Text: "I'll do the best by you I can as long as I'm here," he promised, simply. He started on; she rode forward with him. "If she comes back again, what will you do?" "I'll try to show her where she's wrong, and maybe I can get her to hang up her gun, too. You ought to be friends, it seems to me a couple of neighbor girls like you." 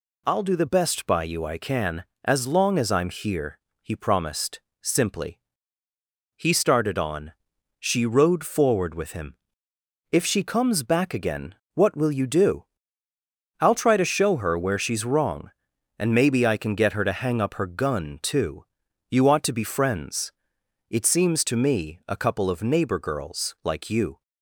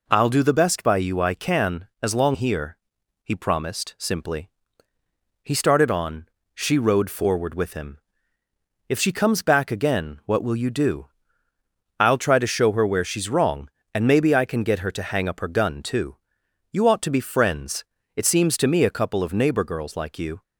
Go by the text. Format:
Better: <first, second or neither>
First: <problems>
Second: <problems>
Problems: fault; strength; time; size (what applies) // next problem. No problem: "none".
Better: first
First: none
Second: skips "as I'm"; at 2.3 s